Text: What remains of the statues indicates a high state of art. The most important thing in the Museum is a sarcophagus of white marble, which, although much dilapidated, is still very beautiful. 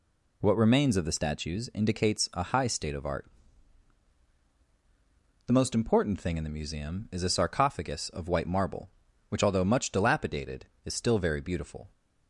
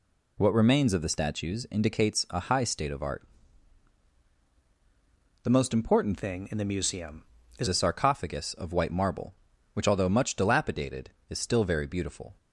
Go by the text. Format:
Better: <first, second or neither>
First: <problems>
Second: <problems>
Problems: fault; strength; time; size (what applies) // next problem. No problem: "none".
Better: first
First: none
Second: changes voice from "thing" to "is"; from 6.1 to 7.6 s; 1.5 s long